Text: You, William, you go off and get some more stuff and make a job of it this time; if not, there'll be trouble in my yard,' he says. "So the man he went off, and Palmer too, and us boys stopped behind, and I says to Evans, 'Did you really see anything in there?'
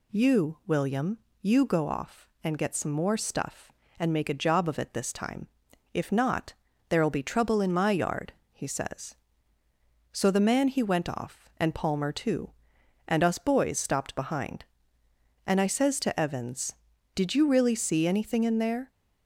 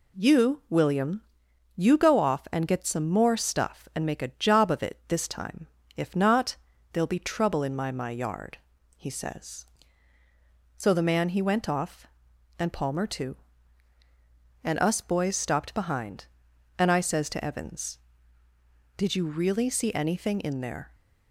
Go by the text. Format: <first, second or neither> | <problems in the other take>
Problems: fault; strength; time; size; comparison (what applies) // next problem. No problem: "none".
first | says "my" twice; at 7.9 s